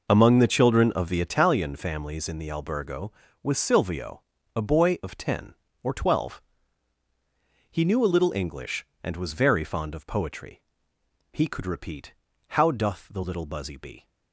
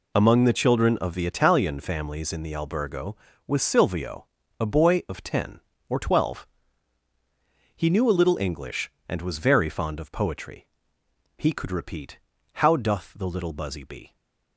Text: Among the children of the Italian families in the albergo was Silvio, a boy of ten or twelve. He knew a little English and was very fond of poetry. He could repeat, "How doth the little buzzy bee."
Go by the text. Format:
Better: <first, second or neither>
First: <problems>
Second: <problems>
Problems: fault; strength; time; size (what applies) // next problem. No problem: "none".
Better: second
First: starts louder than the rest; noticeable; until 1.4 s; 5 dB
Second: none